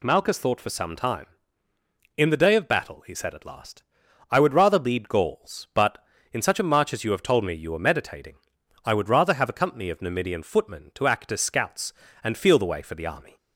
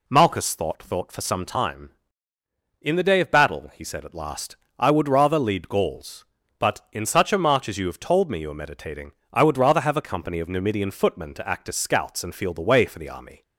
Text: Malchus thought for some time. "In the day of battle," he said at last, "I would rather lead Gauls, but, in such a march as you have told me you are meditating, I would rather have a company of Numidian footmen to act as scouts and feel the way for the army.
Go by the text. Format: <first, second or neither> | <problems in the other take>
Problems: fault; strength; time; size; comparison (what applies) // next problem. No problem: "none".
first | says "thought" twice; at 0.8 s